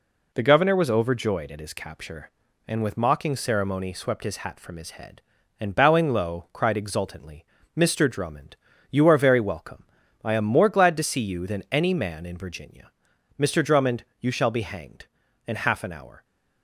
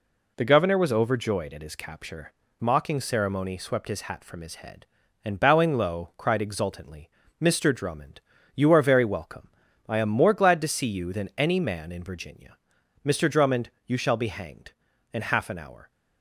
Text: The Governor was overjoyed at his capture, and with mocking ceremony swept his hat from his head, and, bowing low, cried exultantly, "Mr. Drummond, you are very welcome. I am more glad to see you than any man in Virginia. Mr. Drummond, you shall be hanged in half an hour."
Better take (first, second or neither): first